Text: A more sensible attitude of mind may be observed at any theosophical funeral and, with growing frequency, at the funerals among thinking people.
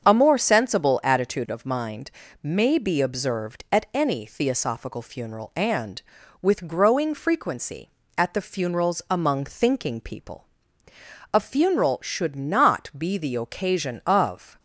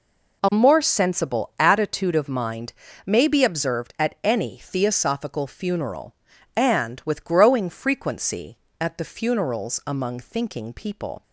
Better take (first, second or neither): second